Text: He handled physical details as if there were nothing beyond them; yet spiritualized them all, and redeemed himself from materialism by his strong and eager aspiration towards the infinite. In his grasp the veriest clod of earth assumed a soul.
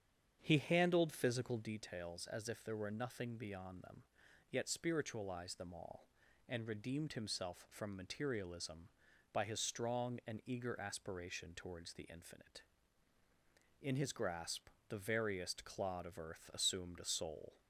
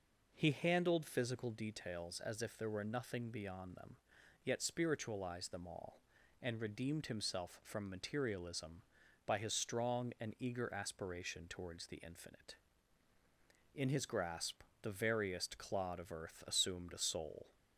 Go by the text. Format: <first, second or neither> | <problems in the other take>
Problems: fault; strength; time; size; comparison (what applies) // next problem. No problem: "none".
second | starts louder than the rest; strong; until 1.7 s; 8.5 dB // pauses between "grasp" and "the"; slight; at 14.6 s; 0.20 s long; slight in the second